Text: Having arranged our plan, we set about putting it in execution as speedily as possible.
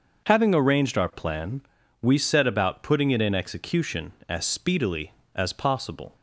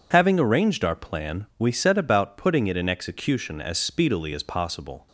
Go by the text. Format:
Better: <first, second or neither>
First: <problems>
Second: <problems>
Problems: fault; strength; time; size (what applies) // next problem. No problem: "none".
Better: neither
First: none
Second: none